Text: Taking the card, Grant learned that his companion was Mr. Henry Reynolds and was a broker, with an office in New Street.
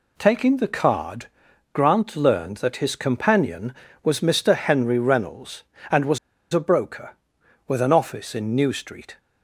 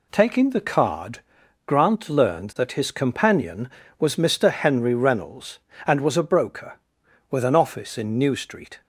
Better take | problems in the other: second | pauses between "was" and "a"; slight; at 6.1 s; 0.35 s long

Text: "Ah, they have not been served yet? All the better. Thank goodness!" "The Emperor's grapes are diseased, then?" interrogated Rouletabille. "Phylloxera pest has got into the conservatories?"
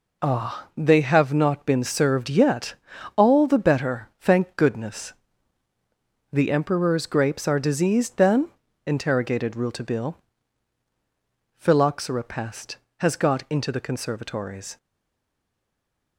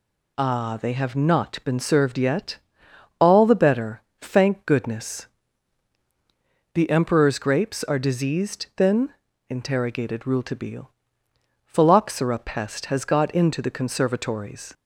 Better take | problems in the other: second | stays silent after the last word; noticeable; from 14.7 s on; 1.4 s long

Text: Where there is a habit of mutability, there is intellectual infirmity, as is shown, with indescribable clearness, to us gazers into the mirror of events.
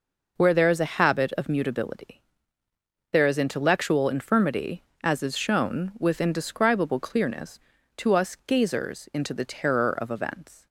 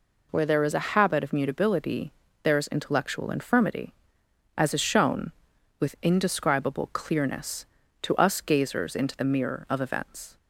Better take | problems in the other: second | says "terror" for "mirror"; at 9.4 s

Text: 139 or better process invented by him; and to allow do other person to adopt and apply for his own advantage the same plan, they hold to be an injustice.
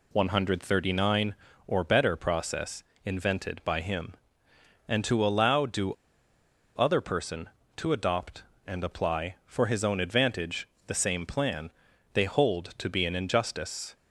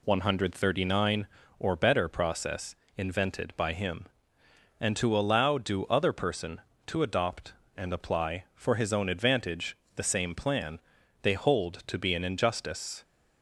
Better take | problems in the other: second | pauses between "process" and "invented"; slight; at 2.8 s; 0.22 s long; slight in the second // pauses between "do" and "other"; noticeable; at 5.9 s; 0.81 s long // pauses between "advantage" and "the"; slight; at 10.6 s; 0.20 s long; slight in the second

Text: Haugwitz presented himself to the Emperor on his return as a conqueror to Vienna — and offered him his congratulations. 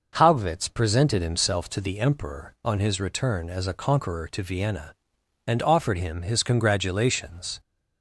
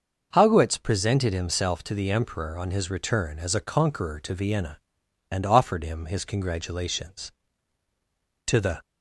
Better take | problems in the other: first | starts louder than the rest; noticeable; until 1.3 s; 6 dB // goes on to say "To the"; slight; from 8.4 s on; 0.34 s long

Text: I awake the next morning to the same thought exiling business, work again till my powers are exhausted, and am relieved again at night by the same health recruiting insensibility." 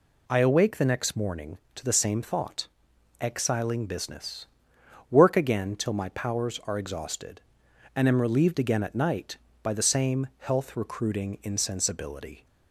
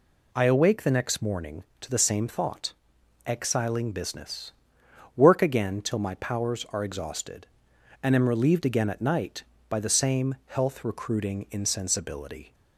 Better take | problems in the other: neither | pauses between "thought" and "exiling"; noticeable; the same in both

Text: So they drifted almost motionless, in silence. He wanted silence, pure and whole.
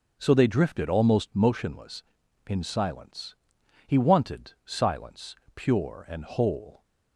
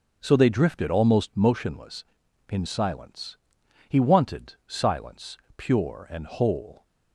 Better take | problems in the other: neither | starts louder than the rest; the same in both

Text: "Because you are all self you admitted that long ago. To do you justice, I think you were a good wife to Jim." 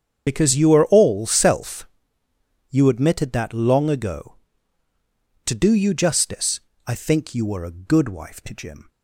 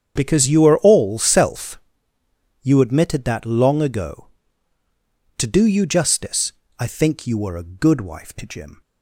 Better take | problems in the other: second | loses the start of "Because"; at 0.2 s; 35 ms // starts louder than the rest; strong; until 1.2 s; 8 dB; strong in the second // pauses between "self" and "you"; noticeable; at 1.8 s; 0.84 s long; noticeable in the second

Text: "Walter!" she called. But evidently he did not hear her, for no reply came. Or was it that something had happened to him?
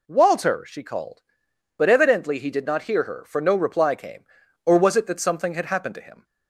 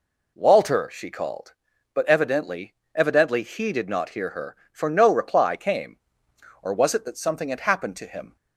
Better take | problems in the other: first | says "evidently" twice; at 2.9 s

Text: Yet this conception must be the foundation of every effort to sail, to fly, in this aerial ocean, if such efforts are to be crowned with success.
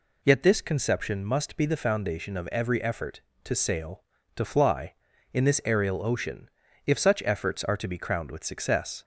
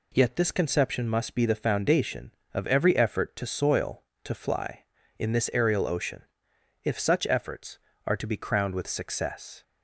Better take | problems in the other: first | says "soil" for "sail"; at 3.4 s

